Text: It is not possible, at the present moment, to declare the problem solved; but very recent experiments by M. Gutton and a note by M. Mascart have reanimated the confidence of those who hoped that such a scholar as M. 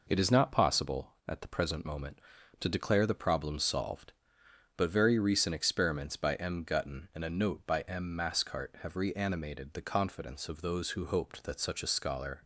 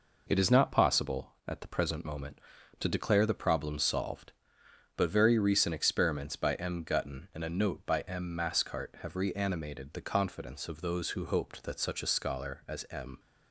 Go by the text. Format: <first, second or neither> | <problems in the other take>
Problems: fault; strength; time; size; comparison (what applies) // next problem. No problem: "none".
second | stops before "as M"; at 12.4 s